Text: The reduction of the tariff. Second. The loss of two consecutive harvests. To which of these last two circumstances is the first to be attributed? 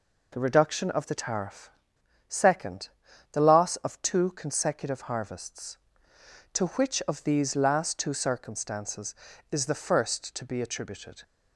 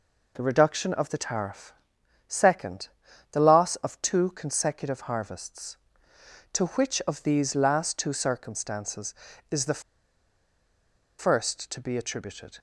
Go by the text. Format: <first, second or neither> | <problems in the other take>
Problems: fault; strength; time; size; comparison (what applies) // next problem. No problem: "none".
first | pauses between "the" and "first"; strong; at 9.8 s; 1.3 s long